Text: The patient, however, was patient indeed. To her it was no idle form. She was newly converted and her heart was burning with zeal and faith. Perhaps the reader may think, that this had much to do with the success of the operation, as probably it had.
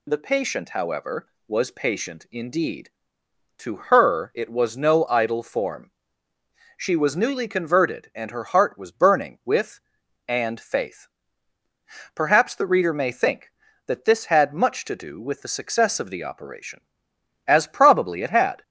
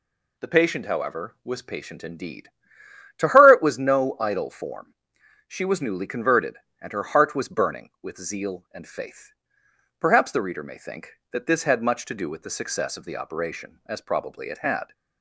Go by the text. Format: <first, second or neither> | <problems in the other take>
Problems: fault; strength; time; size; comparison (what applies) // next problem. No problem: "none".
second | skips "zeal"; at 10.0 s